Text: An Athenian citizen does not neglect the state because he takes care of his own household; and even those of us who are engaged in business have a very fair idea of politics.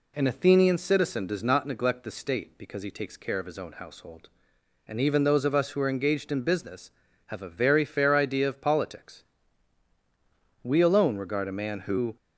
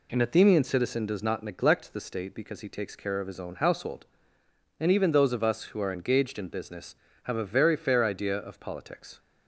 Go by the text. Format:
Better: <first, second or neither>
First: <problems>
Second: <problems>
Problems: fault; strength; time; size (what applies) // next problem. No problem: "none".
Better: second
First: goes on to say "We alone regard a man who"; from 10.6 s on; 1.5 s long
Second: none